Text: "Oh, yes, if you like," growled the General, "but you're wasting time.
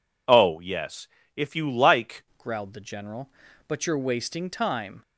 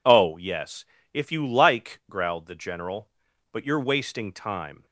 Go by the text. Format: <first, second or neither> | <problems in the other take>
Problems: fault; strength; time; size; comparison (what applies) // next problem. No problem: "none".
second | changes voice at "growled"; from 2.3 s on; 2.7 s long